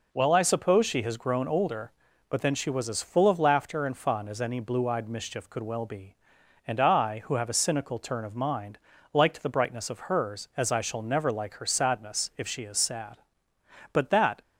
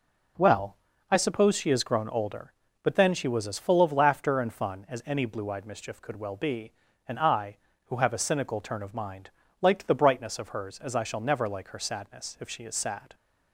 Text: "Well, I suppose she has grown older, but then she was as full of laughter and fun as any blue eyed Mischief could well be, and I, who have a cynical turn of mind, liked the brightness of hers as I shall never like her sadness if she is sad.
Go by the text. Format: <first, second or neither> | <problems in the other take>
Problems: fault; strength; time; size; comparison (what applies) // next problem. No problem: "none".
second | goes on to say "But that"; slight; from 13.9 s on; 0.48 s long